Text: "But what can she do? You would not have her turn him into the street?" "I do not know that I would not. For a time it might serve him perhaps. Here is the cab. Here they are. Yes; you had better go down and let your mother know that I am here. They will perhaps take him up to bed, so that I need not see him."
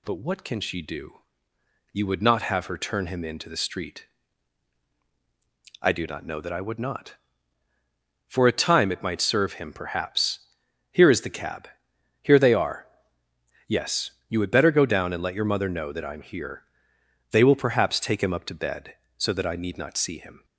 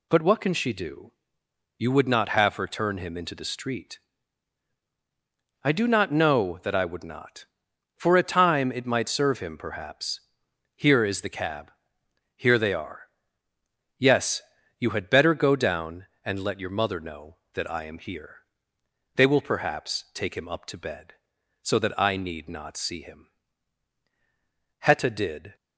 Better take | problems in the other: first | goes on to say "Hetta did"; noticeable; from 24.7 s on; 0.76 s long

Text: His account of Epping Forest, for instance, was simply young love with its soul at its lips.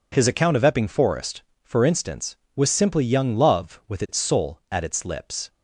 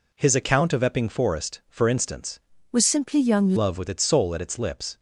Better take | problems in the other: first | changes voice from "was" to "young"; from 2.7 to 3.5 s; 0.8 s long

